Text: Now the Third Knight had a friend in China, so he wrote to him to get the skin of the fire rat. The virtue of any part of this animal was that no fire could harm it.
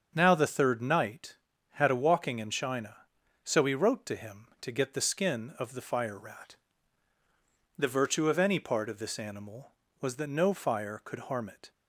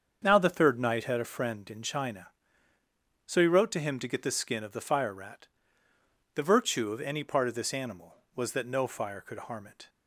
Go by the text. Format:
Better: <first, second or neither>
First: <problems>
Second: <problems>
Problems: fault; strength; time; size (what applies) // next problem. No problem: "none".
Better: second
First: starts louder than the rest; until 1.1 s; 7 dB // says "walking" for "friend"; at 1.9 s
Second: starts louder than the rest; until 1.2 s; 7 dB